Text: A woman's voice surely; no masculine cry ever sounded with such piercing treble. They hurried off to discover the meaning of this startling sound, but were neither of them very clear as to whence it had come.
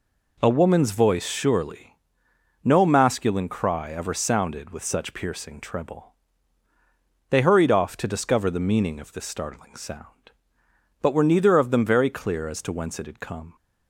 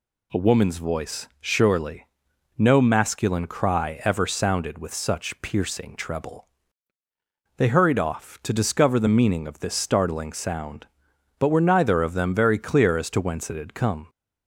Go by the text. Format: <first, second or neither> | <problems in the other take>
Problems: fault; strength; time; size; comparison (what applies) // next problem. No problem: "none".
neither | none